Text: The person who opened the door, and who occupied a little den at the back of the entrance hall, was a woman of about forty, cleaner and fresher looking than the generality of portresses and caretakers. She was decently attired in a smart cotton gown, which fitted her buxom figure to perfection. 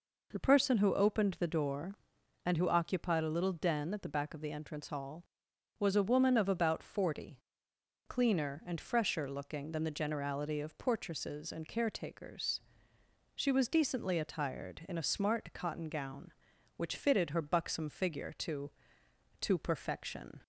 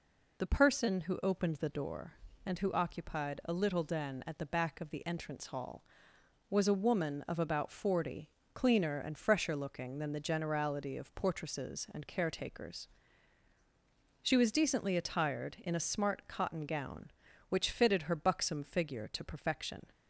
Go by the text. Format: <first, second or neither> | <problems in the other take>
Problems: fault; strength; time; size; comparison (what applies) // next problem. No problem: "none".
second | says "to" twice; at 19.4 s